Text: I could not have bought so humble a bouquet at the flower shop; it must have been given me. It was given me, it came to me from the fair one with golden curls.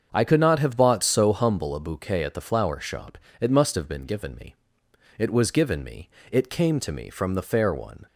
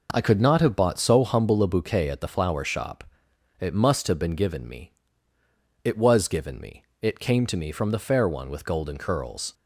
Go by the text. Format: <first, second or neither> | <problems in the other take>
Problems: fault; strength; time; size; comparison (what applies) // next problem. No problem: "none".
second | starts louder than the rest; until 1.1 s; 7 dB // stops before "with golden curls"; at 8.0 s